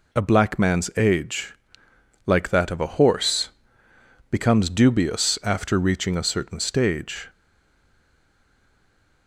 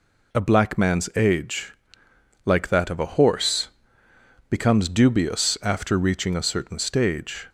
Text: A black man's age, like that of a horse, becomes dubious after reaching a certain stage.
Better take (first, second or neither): second